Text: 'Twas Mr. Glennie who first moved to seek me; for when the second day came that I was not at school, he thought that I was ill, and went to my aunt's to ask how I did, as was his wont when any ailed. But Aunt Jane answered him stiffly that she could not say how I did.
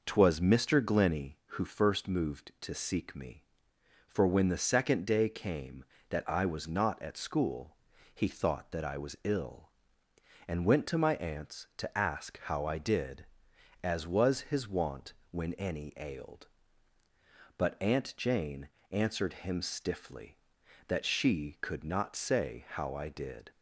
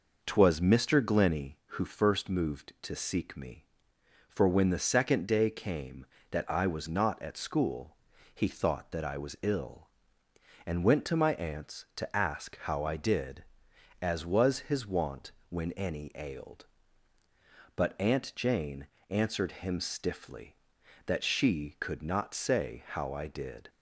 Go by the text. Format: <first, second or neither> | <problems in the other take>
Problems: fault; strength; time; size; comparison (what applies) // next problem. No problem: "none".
neither | pauses between "wont" and "when"; slight; the same in both // pauses between "Jane" and "answered"; slight; the same in both